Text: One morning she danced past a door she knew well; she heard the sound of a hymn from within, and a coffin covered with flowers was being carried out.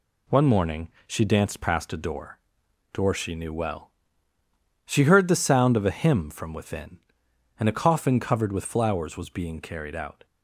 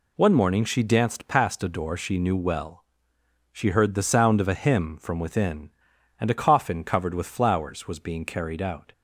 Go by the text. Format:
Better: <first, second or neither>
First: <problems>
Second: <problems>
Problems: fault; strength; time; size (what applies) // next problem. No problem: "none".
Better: second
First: pauses between "morning" and "she"; slight; at 0.8 s; 0.18 s long // says "door" twice; at 2.9 s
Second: none